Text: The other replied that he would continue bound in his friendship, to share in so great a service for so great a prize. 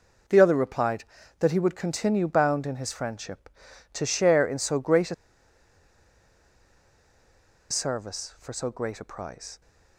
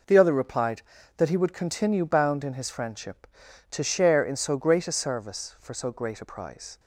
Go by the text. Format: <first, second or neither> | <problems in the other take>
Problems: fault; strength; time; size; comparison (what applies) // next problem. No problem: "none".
second | pauses between "a" and "service"; strong; at 5.1 s; 2.5 s long